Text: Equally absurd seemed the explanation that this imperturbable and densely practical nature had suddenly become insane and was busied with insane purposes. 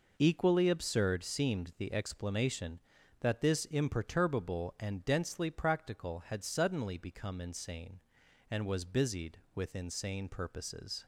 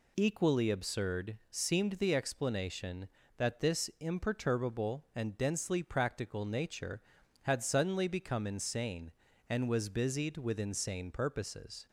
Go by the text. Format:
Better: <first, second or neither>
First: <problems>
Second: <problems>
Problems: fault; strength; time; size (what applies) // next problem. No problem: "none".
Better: second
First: skips "nature"; at 6.2 s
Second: none